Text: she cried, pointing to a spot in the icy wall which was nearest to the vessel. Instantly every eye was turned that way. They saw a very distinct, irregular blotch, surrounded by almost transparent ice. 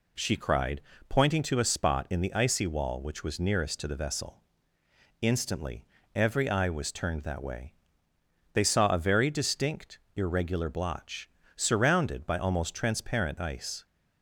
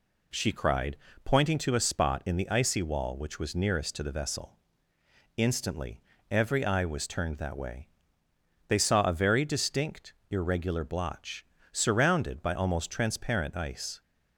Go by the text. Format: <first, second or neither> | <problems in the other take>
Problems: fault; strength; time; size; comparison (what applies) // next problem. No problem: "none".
neither | pauses between "Instantly" and "every"; slight; the same in both